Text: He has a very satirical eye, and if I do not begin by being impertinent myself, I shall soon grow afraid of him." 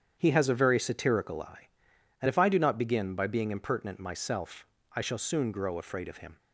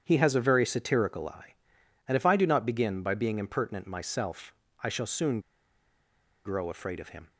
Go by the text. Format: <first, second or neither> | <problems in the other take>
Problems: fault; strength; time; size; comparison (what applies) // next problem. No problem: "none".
first | starts louder than the rest; strong; until 1.0 s; 8.5 dB; strong in the first // pauses between "soon" and "grow"; at 5.3 s; 1.0 s long